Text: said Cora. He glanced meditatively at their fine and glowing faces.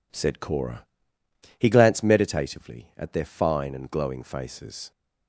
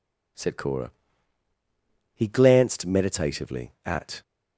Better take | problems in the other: first | stops before "their fine and glowing faces"; at 4.2 s

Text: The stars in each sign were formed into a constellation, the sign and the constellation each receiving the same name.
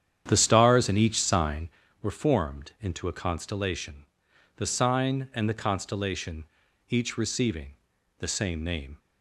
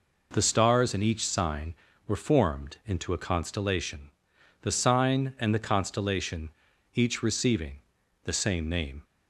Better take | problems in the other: second | starts louder than the rest; strong; until 1.8 s; 9 dB // pauses between "constellation" and "each"; at 6.4 s; 0.44 s long; also in the second // pauses between "receiving" and "the"; at 7.7 s; 0.44 s long; also in the second

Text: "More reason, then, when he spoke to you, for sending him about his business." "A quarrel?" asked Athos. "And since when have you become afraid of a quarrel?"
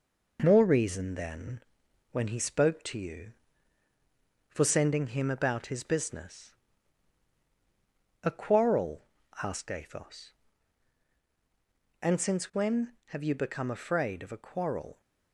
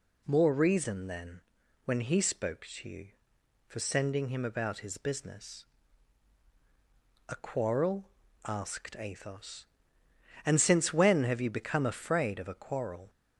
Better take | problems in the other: second | gets quieter; throughout; 3.5 dB

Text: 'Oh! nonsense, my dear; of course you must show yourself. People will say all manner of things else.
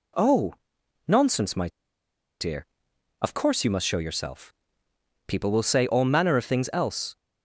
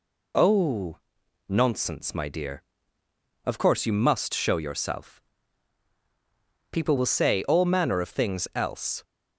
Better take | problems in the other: second | pauses between "my" and "dear"; noticeable; at 1.6 s; 0.72 s long

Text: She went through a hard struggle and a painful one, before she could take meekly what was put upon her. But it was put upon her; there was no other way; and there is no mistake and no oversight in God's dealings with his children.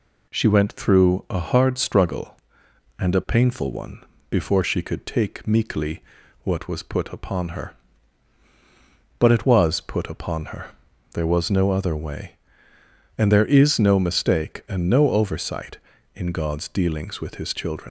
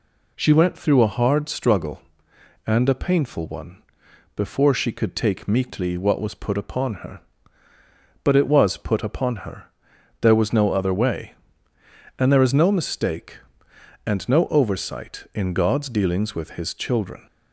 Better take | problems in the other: second | pauses between "meekly" and "what"; at 6.0 s; 0.40 s long // leaves "children" unfinished; at 17.8 s; 160 ms

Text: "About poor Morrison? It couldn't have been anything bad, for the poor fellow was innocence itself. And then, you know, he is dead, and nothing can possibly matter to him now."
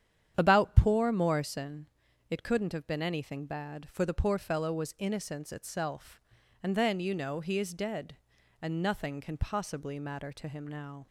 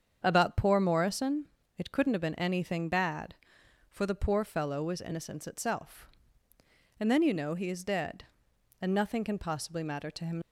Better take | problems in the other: first | starts louder than the rest; strong; until 1.2 s; 7.5 dB; strong in the first // stops before "now"; at 10.4 s

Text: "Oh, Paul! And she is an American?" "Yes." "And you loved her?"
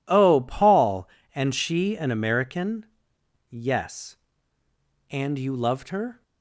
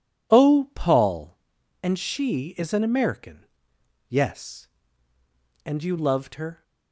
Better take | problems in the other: second | skips "is"; at 1.9 s

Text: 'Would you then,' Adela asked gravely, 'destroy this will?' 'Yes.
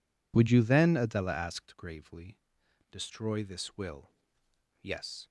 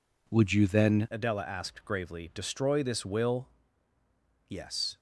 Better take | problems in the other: first | changes voice at "Adela"; from 1.1 s on; 3.8 s long

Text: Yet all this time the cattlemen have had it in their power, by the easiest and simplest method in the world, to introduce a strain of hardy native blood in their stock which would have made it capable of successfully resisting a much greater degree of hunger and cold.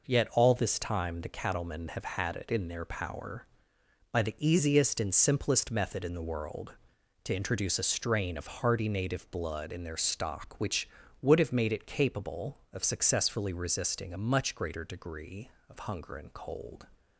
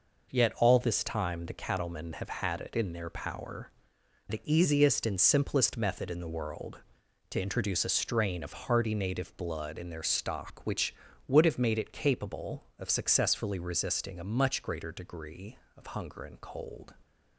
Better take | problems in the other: first | skips "by"; at 4.0 s

